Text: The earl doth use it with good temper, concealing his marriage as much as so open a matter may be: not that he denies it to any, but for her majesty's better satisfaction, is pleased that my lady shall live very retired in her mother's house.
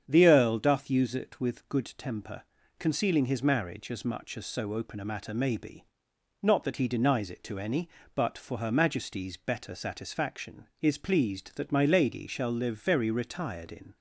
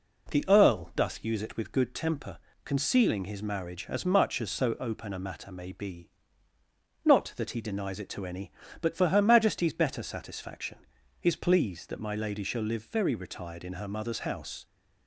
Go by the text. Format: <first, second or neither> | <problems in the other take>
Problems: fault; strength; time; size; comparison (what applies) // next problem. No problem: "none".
second | starts louder than the rest; strong; until 1.0 s; 8 dB // stops before "her mother's house"; at 13.9 s